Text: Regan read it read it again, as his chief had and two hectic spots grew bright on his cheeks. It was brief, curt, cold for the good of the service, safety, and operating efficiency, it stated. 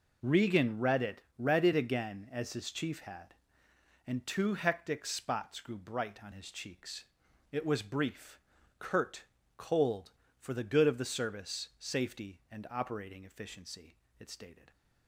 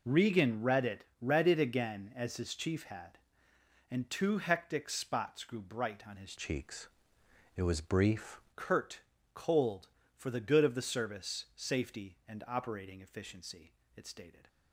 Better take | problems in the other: first | pauses between "it" and "read"; slight; at 1.0 s; 0.18 s long; slight in the first // changes voice from "cheeks" to "brief"; from 6.3 to 8.4 s; 2.1 s long

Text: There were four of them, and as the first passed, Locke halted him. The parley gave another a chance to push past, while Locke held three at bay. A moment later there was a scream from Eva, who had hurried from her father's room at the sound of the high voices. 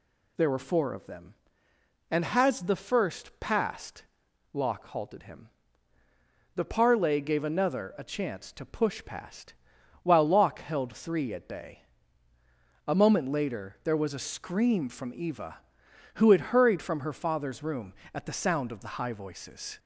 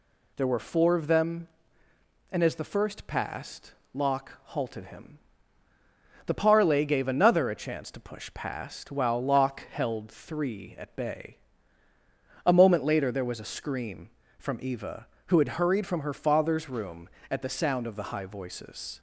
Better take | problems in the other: second | says "has" for "as"; at 2.2 s

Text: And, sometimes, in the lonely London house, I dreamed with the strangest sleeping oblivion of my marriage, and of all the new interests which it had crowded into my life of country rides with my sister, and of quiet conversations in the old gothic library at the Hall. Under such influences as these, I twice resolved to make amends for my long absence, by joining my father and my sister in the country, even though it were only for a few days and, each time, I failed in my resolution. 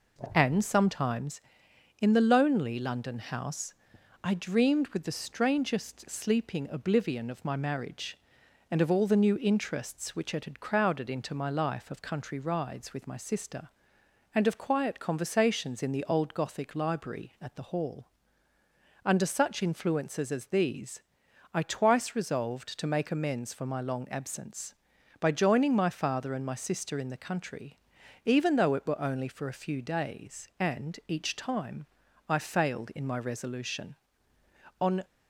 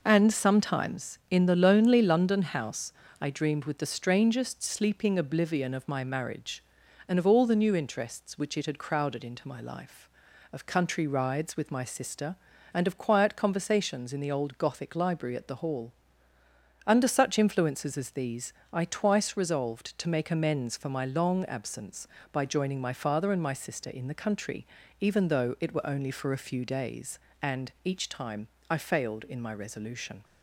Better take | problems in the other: second | goes on to say "On"; slight; from 34.8 s on; 0.22 s long

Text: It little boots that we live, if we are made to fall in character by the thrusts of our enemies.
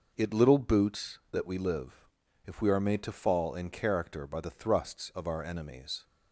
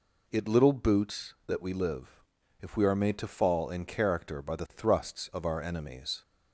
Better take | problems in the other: second | gets quieter; noticeable; throughout; 5.5 dB

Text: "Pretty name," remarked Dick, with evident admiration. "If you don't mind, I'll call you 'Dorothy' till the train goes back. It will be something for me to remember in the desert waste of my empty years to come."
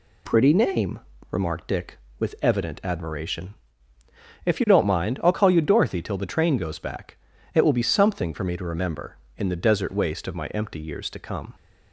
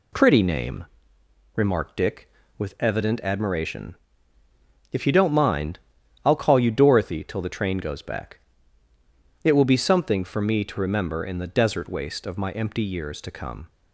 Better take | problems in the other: neither | none

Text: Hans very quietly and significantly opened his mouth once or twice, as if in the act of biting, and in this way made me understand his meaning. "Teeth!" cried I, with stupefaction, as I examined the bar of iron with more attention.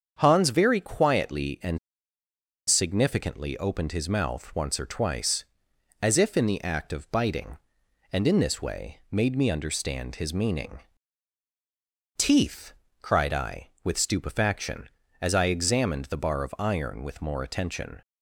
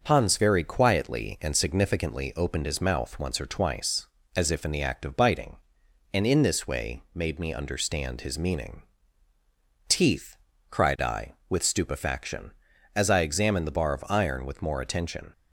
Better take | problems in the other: second | starts louder than the rest; strong; until 1.2 s; 7.5 dB // pauses between "and" and "significantly"; noticeable; at 1.7 s; 0.88 s long

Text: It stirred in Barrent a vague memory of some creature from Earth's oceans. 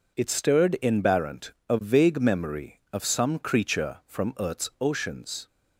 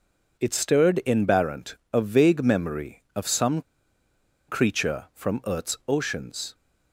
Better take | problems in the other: first | pauses between "Barrent" and "a"; slight; at 1.7 s; 0.18 s long; slight in the first // pauses between "some" and "creature"; noticeable; at 3.6 s; 0.86 s long

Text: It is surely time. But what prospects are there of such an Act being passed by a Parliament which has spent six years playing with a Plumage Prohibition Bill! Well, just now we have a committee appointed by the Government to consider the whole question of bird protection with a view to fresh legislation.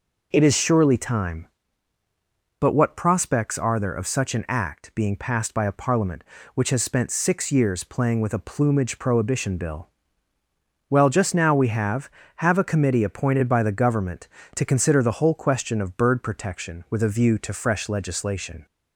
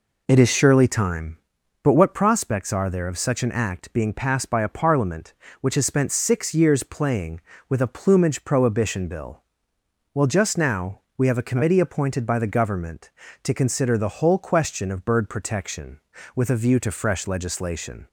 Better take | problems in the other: second | says "have" twice; at 12.3 s

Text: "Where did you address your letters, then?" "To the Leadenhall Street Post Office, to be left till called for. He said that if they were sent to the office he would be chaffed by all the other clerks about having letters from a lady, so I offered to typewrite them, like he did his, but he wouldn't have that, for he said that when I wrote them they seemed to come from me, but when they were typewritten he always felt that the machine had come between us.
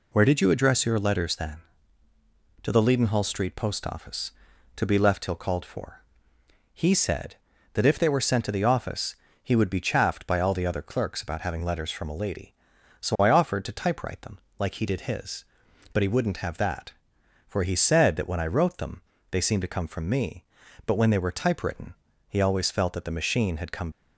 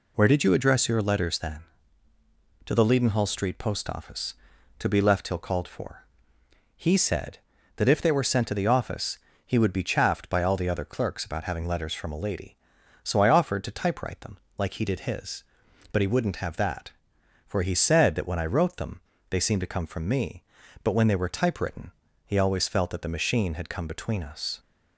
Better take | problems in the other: second | pauses between "office" and "he"; slight; at 9.1 s; 0.28 s long; slight in the second // pauses between "them" and "they"; slight; at 19.0 s; 0.30 s long; slight in the second // pauses between "typewritten" and "he"; slight; at 21.9 s; 0.34 s long; slight in the second // stops before "between us"; at 23.9 s

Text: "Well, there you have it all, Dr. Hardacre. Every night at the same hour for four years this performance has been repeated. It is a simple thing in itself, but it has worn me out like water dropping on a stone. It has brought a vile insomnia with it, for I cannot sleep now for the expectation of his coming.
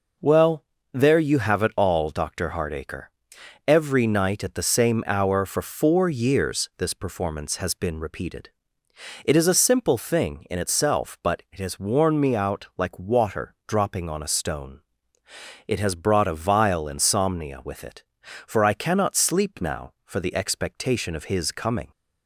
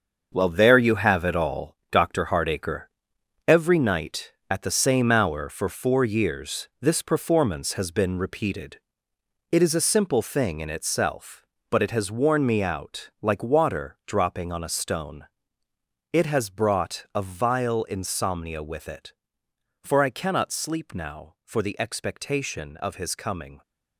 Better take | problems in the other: first | gets quieter; strong; throughout; 9 dB

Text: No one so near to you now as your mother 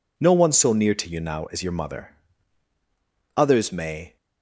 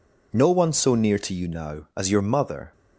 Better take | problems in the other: second | goes on to say "Others may"; noticeable; from 3.3 s on; 0.80 s long

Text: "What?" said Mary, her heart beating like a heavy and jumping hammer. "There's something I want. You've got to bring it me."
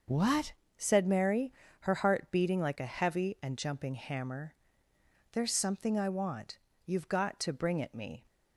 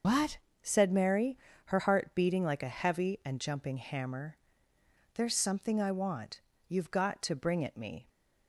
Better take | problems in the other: first | loses the start of "What"; at 0.0 s; 120 ms // starts louder than the rest; noticeable; until 1.3 s; 6 dB; also in the first

